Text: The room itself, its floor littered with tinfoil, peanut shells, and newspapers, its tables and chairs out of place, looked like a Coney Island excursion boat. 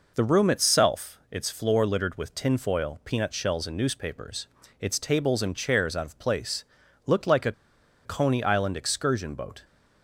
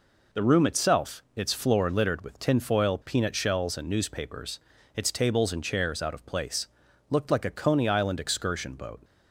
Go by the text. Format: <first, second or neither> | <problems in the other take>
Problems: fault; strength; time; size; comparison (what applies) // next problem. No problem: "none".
second | pauses between "a" and "Coney"; noticeable; at 7.5 s; 0.53 s long